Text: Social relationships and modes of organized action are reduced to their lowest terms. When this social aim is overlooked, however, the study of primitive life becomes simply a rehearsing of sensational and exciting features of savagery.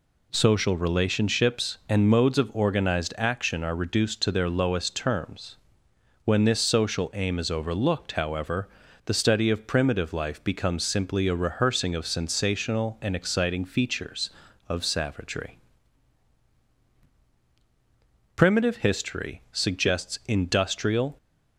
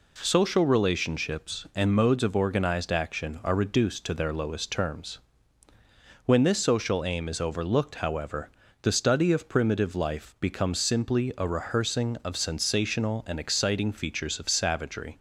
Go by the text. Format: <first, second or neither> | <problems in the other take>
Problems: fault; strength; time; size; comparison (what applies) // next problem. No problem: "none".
second | goes on to say "Primitive history suggests industrial"; strong; from 18.3 s on; 2.8 s long